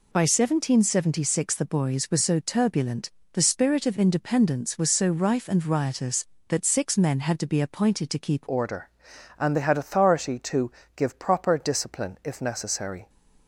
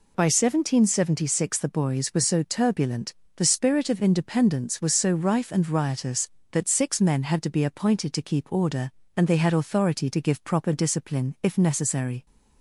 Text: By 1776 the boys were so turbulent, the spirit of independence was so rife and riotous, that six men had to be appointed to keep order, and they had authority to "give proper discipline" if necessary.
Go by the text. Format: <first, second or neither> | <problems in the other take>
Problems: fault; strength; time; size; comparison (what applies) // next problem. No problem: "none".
second | changes voice at "order"; from 8.4 s on; 4.6 s long // pauses between "to" and "give"; slight; at 10.7 s; 0.24 s long